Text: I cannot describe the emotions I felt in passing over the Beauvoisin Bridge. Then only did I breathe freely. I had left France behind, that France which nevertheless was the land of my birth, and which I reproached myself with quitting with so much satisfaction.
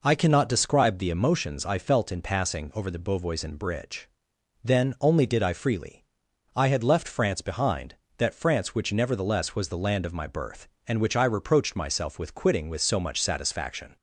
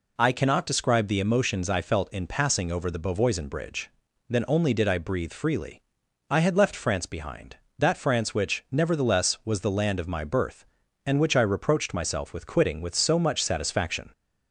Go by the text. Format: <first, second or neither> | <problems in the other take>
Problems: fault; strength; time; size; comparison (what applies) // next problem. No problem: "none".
second | skips "breathe"; at 5.5 s